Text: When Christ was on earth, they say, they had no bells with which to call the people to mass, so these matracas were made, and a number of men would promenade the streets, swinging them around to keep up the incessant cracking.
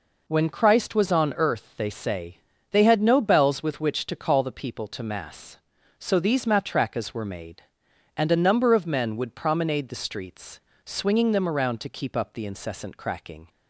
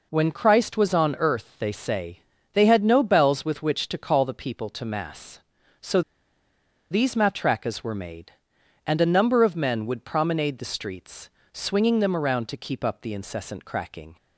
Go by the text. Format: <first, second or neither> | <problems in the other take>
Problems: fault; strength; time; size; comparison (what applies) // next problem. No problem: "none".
first | pauses between "so" and "these"; noticeable; at 6.0 s; 0.90 s long